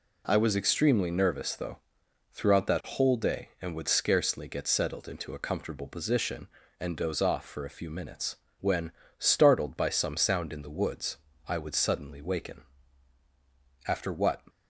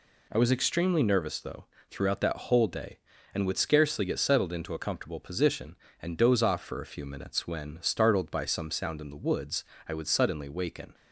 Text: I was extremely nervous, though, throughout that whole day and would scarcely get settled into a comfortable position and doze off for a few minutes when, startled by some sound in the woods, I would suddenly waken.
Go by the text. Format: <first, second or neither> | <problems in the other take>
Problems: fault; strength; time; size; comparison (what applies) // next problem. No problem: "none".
second | pauses between "minutes" and "when"; slight; at 8.3 s; 0.26 s long // goes on to say "After what"; from 13.8 s on; 0.56 s long